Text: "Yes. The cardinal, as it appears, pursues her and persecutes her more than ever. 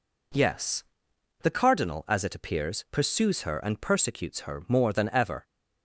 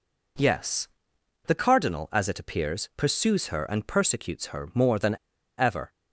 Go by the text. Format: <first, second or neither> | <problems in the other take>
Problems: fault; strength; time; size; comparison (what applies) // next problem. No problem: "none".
first | pauses between "than" and "ever"; at 5.1 s; 0.42 s long